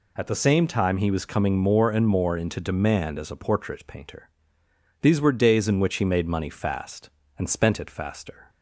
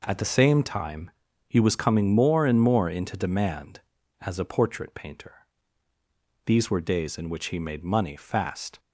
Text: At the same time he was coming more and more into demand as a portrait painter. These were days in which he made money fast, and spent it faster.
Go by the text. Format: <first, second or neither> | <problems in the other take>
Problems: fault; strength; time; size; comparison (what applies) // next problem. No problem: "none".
first | pauses between "time" and "he"; slight; at 1.1 s; 0.36 s long // stops before "and spent it faster"; at 8.7 s